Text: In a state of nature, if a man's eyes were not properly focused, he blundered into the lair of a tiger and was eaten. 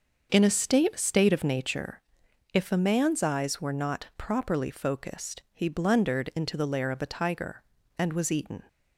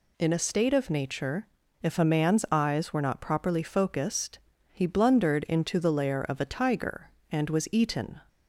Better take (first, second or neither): second